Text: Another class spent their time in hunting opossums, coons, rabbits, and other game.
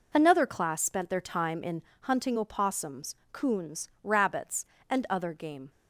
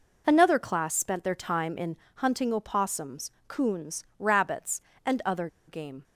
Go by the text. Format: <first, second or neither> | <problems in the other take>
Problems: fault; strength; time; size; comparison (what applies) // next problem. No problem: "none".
first | pauses between "in" and "hunting"; slight; at 1.9 s; 0.20 s long; slight in the first // pauses between "other" and "game"; slight; at 5.4 s; 0.20 s long